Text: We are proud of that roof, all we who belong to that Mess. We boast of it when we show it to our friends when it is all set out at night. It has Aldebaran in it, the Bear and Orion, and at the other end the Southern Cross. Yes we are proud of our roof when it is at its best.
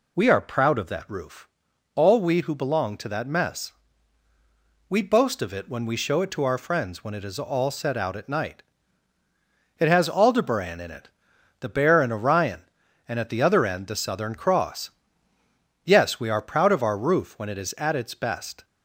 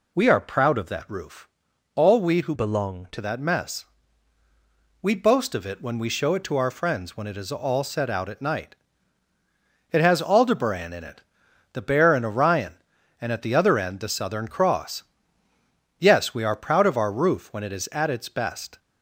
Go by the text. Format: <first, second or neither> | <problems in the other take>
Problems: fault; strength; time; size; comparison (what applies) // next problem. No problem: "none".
first | changes voice from "belong" to "to"; from 2.5 to 3.1 s; 0.6 s long